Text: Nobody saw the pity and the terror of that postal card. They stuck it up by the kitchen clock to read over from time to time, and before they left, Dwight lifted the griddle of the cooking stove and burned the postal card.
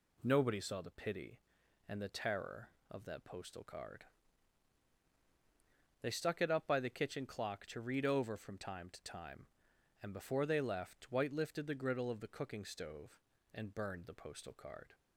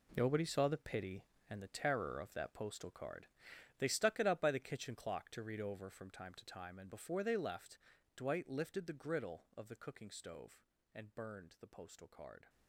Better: first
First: none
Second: gets quieter; strong; throughout; 13.5 dB

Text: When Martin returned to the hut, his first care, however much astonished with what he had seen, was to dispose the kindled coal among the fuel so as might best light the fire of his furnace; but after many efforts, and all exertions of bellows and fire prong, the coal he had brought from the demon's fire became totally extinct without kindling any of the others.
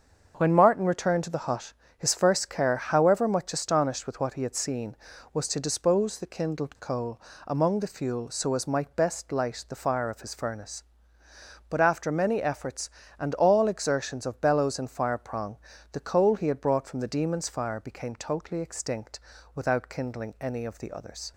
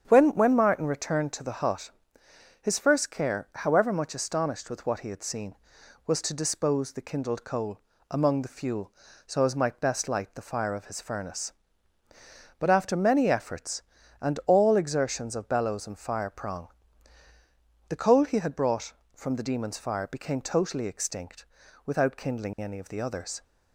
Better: first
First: starts louder than the rest; until 1.3 s; 7 dB // pauses between "coal" and "among"; slight; at 7.2 s; 0.28 s long // pauses between "extinct" and "without"; at 19.1 s; 0.38 s long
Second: starts louder than the rest; strong; until 1.1 s; 8 dB // says "When" twice; at 0.3 s // pauses between "coal" and "among"; slight; at 7.7 s; 0.28 s long // pauses between "extinct" and "without"; at 21.4 s; 0.38 s long

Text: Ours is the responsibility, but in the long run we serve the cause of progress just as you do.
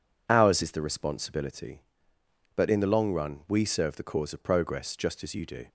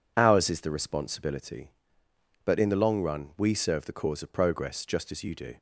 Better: neither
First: none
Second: none

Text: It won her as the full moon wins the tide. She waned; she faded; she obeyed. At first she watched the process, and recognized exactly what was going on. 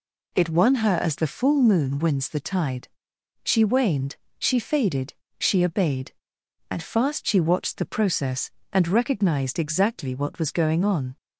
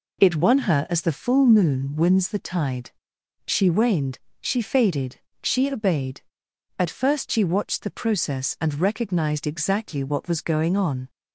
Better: second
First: says "fast" for "first"; at 6.8 s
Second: none

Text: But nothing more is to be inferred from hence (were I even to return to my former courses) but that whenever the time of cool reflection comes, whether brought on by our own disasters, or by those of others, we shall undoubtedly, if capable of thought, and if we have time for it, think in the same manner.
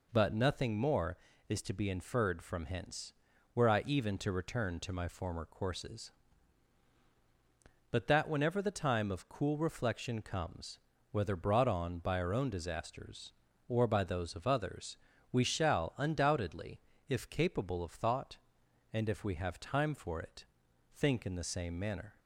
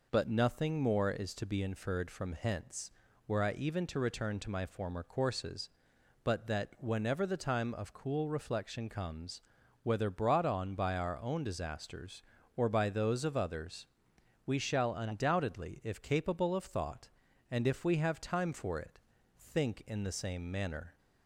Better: neither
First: none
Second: none

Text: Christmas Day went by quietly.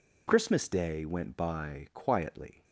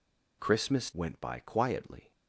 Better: first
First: none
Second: skips "Day"; at 0.9 s

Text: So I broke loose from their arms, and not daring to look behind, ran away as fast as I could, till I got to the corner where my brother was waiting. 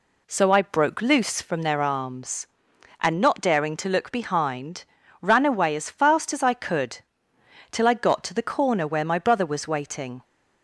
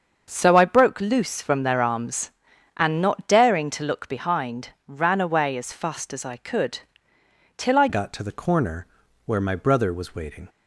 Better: first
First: none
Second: starts louder than the rest; until 1.3 s; 6.5 dB // changes voice at "got"; from 7.8 s on; 2.6 s long // pauses between "corner" and "where"; at 8.8 s; 0.40 s long

